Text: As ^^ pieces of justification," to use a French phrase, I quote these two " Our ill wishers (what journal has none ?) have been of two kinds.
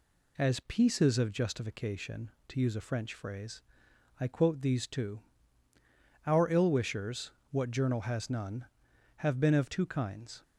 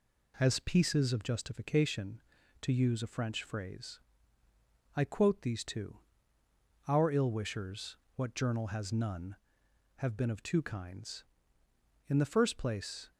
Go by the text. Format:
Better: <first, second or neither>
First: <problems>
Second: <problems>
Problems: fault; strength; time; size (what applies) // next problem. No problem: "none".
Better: first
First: none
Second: goes on to say "In the first place"; noticeable; from 12.0 s on; 1.0 s long